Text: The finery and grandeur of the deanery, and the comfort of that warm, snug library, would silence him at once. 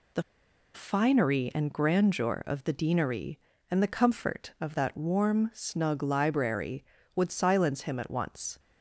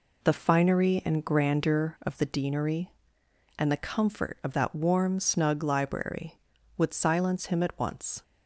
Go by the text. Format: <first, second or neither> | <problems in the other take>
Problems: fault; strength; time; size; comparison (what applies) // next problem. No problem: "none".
second | pauses between "The" and "finery"; noticeable; at 0.2 s; 0.53 s long